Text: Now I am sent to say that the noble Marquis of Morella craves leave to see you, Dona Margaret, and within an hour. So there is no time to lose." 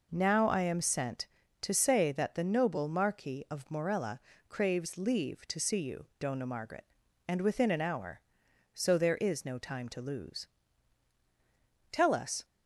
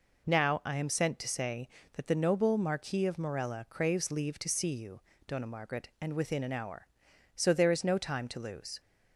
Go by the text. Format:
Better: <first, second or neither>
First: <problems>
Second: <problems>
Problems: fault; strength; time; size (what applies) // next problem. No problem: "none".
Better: second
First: pauses between "Morella" and "craves"; slight; at 4.2 s; 0.28 s long // goes on to say "Tell us"; from 11.9 s on; 0.54 s long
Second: none